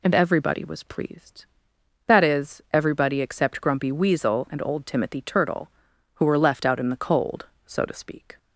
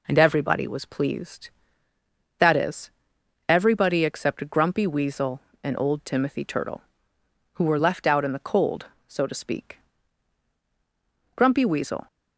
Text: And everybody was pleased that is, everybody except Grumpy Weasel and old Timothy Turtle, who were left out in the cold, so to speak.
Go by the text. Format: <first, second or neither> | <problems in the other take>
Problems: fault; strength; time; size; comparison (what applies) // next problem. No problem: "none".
first | goes on to say "Grumpy Weasel"; noticeable; from 11.3 s on; 0.70 s long